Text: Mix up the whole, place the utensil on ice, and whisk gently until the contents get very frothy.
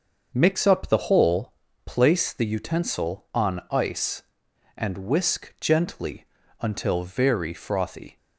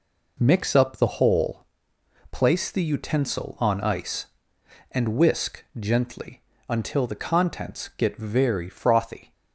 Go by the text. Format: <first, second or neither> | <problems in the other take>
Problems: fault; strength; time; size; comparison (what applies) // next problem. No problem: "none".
second | starts louder than the rest; until 1.3 s; 6.5 dB // pauses between "gently" and "until"; slight; at 6.2 s; 0.34 s long; slight in the second // skips "the contents get"; at 7.0 s